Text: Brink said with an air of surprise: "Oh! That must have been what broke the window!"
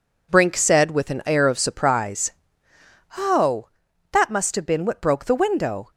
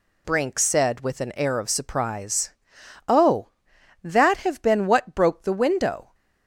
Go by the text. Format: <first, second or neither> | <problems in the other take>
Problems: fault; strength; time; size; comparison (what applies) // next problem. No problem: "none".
first | skips "must"; at 4.3 s